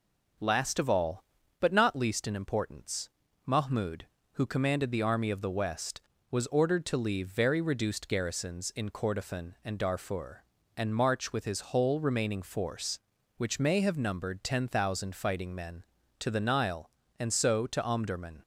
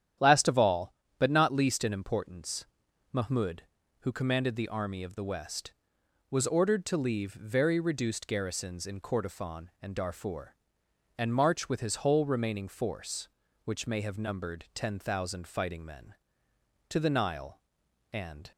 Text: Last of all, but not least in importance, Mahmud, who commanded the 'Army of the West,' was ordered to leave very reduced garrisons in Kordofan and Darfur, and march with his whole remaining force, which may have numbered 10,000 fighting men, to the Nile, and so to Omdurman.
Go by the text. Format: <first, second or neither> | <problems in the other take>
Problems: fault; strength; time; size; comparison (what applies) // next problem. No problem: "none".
first | starts louder than the rest; strong; until 1.4 s; 10 dB // stops before "so to Omdurman"; at 18.5 s